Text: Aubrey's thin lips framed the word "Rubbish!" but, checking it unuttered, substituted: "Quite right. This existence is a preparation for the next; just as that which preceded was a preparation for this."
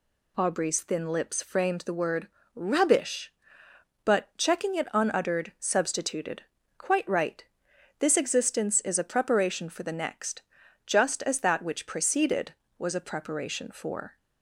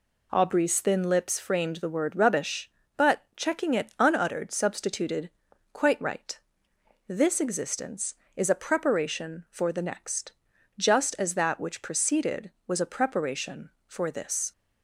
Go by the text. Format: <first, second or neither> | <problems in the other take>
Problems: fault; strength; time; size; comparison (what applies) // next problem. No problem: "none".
second | pauses between "word" and "Rubbish"; slight; at 2.2 s; 0.30 s long // stops before "this"; at 14.1 s